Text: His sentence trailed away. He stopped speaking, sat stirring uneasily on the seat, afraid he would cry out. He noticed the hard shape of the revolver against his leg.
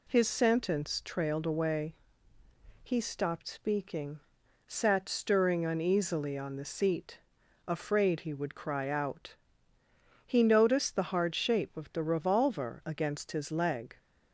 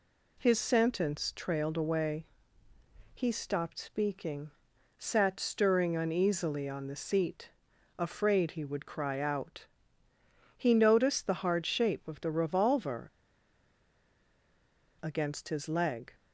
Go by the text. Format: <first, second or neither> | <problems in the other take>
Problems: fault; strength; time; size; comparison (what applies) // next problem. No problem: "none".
first | pauses between "revolver" and "against"; strong; at 13.0 s; 1.9 s long